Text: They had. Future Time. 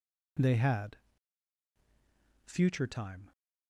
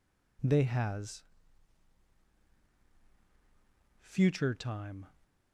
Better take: first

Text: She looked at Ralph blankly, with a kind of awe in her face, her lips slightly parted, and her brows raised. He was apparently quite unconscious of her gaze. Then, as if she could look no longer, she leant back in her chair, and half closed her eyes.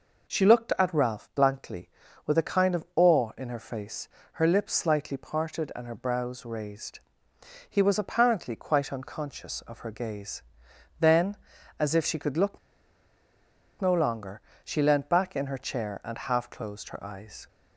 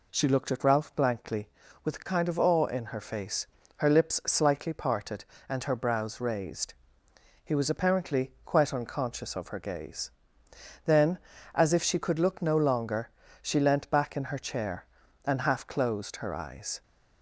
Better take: second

